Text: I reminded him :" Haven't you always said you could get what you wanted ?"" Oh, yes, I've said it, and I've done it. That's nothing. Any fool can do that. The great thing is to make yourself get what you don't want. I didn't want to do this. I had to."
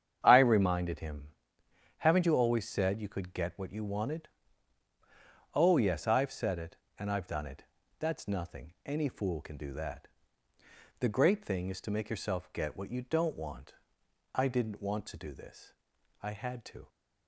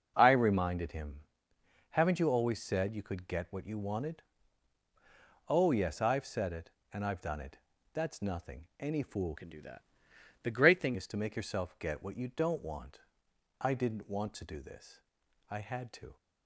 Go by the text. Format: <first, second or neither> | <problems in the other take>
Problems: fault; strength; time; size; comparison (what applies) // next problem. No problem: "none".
first | starts louder than the rest; strong; until 1.1 s; 9.5 dB; strong in the first // changes voice from "can" to "thing"; from 9.3 to 10.9 s; 1.6 s long